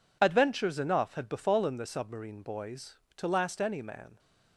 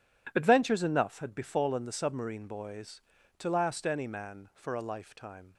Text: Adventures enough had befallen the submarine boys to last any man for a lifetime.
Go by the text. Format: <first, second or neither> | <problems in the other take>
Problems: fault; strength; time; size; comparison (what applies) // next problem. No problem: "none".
second | stops before "for a lifetime"; at 4.1 s